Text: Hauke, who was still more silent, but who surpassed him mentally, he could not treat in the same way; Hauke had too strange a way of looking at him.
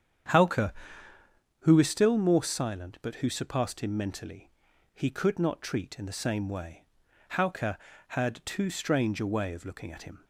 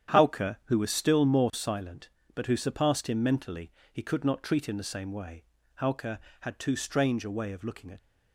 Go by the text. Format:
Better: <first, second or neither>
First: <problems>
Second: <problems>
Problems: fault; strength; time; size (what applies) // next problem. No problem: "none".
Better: first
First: starts louder than the rest; strong; until 2.1 s; 8.5 dB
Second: starts louder than the rest; strong; until 1.2 s; 9.5 dB // stops before "him"; at 7.9 s